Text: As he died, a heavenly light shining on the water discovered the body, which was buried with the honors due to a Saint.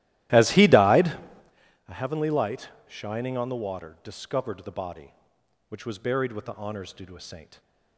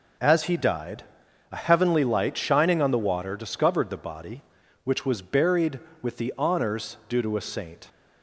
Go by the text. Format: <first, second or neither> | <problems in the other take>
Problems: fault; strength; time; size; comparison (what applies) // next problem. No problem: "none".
second | starts louder than the rest; strong; until 1.5 s; 15 dB // pauses between "light" and "shining"; slight; at 2.6 s; 0.18 s long